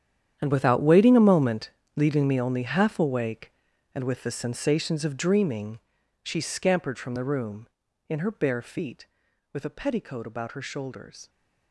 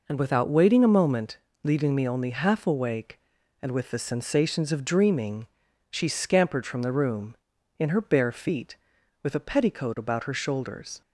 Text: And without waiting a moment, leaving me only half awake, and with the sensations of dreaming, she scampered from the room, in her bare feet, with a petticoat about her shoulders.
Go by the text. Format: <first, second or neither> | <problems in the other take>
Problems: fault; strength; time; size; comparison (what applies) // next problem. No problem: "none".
second | gets quieter; strong; throughout; 15.5 dB